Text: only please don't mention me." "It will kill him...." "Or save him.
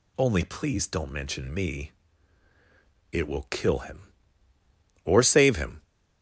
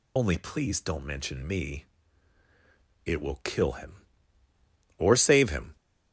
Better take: first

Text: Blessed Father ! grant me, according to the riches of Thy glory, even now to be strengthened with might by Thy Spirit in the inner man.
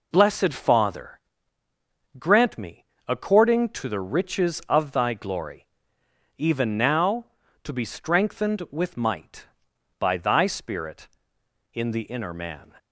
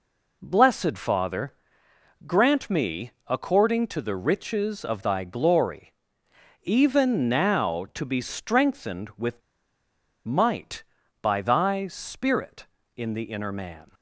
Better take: first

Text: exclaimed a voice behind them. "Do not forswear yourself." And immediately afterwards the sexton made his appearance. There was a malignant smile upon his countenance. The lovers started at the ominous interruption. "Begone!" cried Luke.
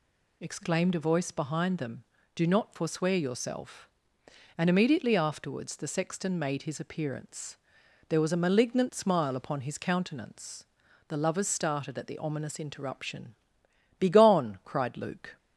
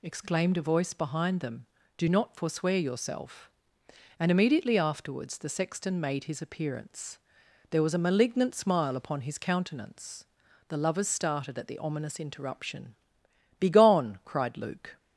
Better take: neither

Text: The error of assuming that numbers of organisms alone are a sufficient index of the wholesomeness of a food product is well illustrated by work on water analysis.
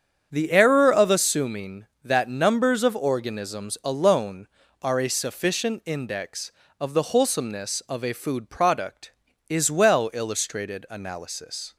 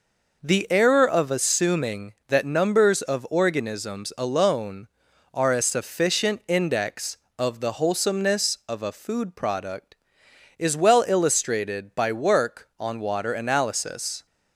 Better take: second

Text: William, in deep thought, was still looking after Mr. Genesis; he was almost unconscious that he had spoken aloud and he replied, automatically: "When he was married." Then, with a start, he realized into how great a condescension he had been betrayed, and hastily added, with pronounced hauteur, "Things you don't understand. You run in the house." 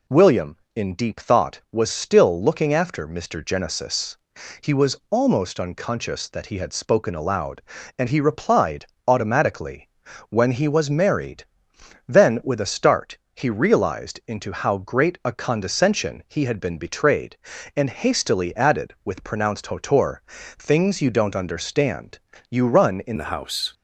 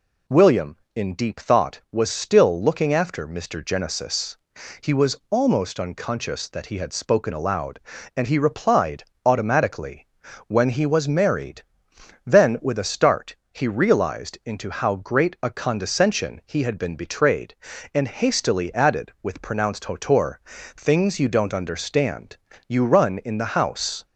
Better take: second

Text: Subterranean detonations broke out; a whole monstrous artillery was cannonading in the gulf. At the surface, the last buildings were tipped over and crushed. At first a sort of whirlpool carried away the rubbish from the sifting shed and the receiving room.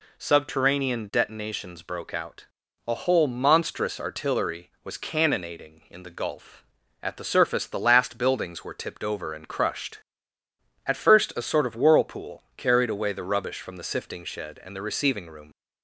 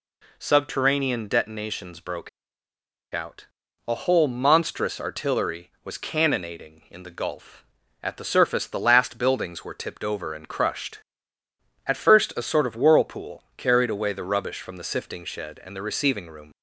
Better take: first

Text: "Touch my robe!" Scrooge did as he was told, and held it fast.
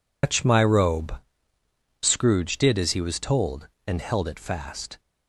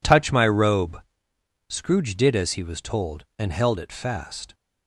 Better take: second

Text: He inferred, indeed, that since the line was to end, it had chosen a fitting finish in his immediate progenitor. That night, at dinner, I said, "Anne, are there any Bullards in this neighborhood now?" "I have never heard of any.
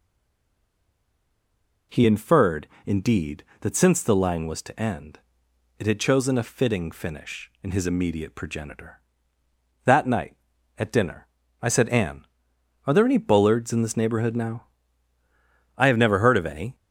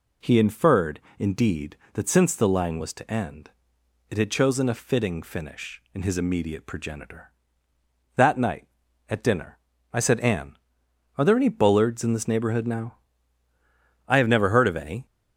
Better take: second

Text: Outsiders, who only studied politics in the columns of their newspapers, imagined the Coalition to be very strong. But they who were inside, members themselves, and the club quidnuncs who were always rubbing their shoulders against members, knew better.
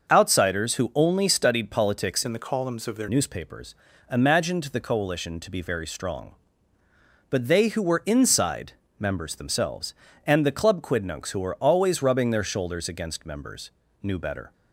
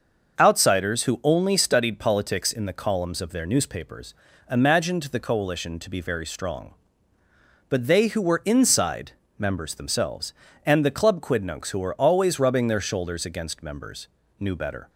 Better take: second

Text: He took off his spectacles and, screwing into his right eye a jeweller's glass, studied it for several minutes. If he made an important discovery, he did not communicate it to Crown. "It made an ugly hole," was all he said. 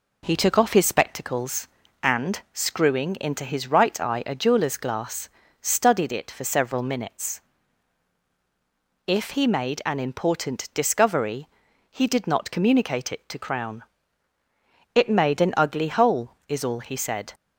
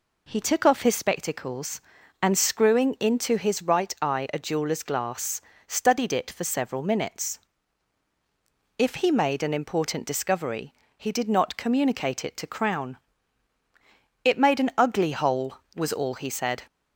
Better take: second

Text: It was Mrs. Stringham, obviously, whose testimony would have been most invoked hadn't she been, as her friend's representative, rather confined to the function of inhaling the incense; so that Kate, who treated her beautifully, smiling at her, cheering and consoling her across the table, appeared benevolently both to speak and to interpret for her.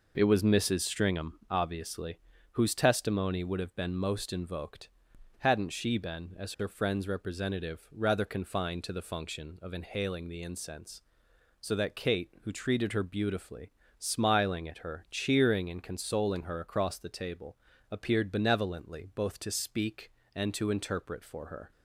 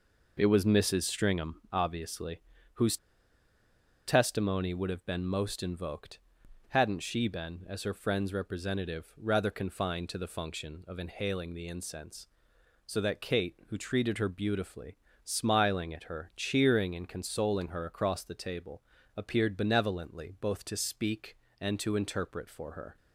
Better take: first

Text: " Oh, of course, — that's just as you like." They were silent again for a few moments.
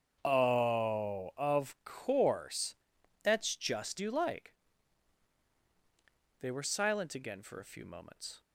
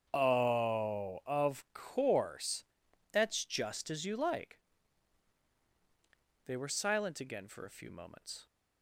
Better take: second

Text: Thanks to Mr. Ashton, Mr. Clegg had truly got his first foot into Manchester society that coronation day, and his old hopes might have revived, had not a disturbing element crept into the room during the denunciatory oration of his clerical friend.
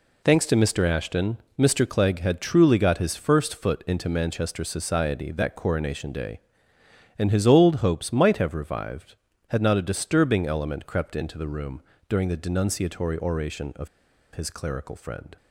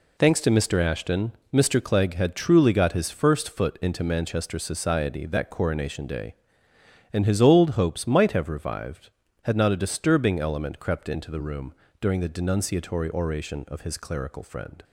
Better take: second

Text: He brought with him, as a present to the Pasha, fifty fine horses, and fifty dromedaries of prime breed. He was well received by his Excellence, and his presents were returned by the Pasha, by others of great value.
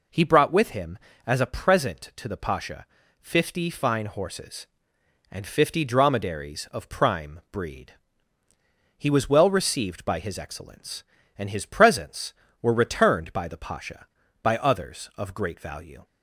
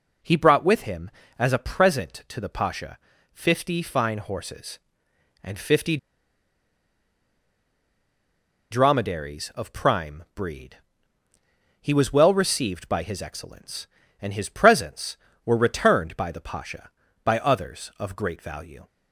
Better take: first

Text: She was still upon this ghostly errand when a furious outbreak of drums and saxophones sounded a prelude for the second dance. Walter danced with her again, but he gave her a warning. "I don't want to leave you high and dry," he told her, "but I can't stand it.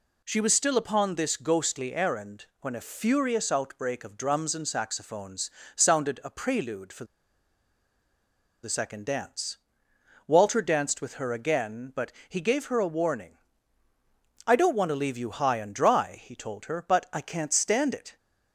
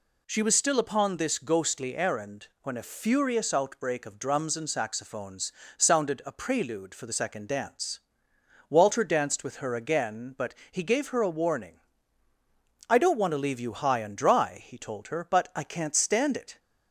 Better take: second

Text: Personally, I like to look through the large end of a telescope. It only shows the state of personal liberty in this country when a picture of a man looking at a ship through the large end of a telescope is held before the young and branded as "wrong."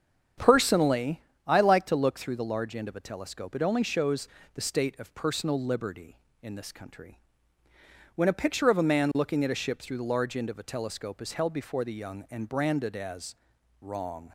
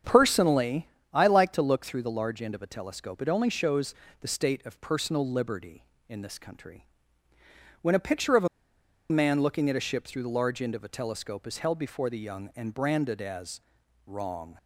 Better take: first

